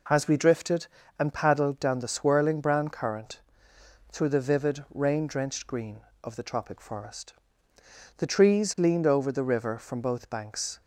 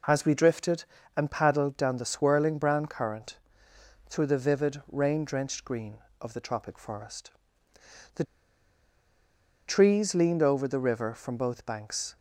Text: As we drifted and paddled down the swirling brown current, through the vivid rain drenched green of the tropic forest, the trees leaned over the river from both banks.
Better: first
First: none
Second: pauses between "the" and "trees"; strong; at 8.2 s; 1.4 s long

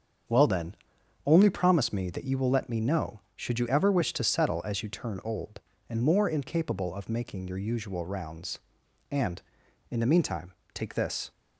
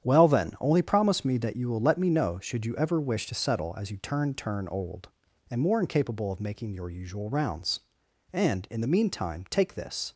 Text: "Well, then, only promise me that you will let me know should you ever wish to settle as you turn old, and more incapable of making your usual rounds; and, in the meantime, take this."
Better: first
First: starts louder than the rest; strong; until 1.7 s; 7 dB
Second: starts louder than the rest; strong; until 1.1 s; 9.5 dB // says "turn" twice; at 4.3 s

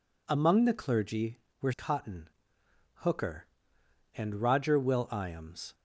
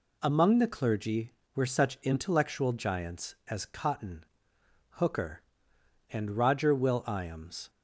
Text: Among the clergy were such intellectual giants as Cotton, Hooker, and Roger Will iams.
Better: second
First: skips "such intellectual giants as"; at 1.7 s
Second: none

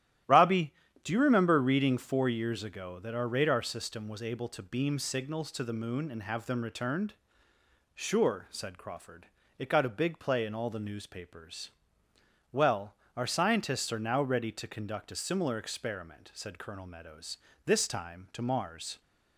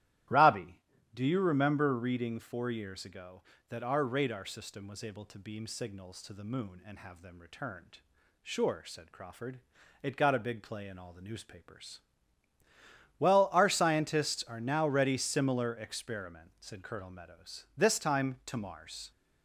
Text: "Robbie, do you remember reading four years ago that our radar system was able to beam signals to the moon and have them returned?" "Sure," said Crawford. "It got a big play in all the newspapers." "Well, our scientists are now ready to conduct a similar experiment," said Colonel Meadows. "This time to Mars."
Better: first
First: starts louder than the rest; strong; until 1.5 s; 12.5 dB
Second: starts louder than the rest; strong; until 1.6 s; 13.5 dB // skips "to conduct a"; at 15.1 s

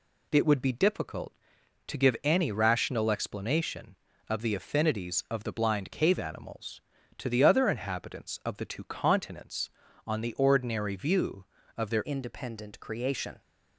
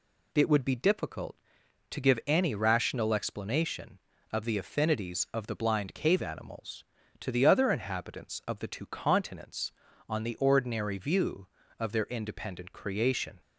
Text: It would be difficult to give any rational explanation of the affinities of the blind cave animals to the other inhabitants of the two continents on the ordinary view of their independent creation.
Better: second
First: changes voice at "independent"; from 12.0 s on; 1.4 s long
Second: none

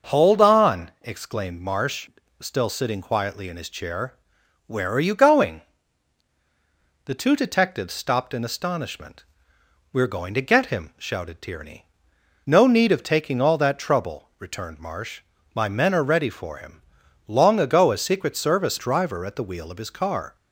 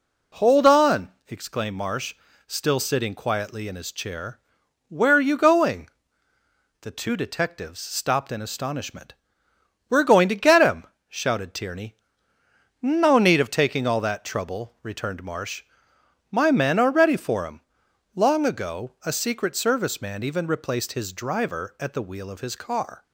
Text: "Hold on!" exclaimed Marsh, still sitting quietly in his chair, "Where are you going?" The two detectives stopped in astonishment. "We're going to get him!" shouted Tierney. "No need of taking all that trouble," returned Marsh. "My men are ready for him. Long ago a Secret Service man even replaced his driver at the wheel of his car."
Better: second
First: starts louder than the rest; noticeable; until 1.1 s; 6 dB // skips "man even replaced his"; at 18.7 s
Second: none

